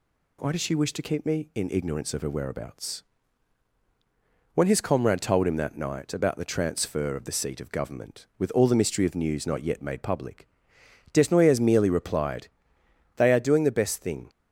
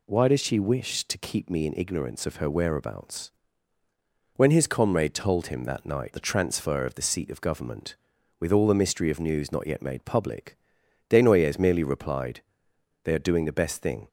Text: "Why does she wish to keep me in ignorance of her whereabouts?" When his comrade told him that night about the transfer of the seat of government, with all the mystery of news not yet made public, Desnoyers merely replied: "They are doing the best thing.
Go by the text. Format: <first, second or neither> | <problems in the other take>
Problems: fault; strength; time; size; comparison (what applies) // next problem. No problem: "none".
first | skips "about"; at 6.1 s